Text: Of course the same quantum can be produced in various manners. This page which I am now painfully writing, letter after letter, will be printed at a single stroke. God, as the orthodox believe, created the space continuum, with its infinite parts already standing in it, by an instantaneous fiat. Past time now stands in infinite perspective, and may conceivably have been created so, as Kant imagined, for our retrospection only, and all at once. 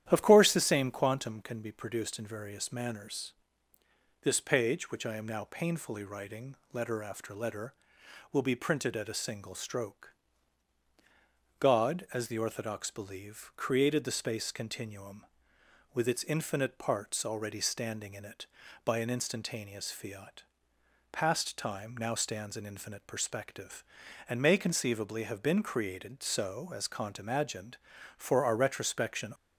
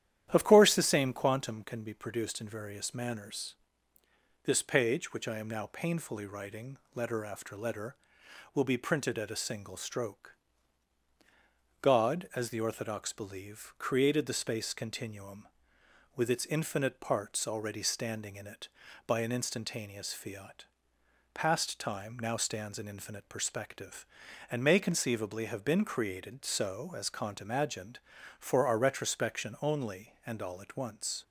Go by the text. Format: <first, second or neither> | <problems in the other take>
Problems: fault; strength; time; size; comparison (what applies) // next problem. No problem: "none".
second | starts louder than the rest; strong; until 1.0 s; 11 dB; strong in the second // stops before "only and all at once"; at 29.3 s